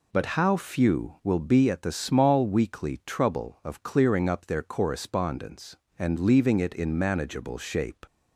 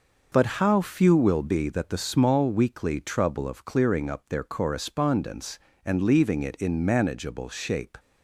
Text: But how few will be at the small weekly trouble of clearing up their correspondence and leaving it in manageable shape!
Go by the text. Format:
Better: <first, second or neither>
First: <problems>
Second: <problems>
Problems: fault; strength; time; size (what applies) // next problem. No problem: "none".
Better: first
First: none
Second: says "that" for "at"; at 1.6 s